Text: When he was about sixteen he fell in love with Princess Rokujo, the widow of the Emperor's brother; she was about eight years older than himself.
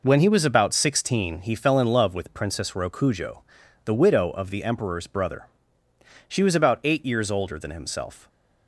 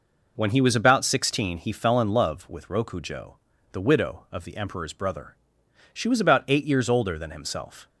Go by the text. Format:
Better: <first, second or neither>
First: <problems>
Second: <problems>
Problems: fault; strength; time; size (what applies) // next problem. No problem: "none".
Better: first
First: none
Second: skips "Princess"; at 2.6 s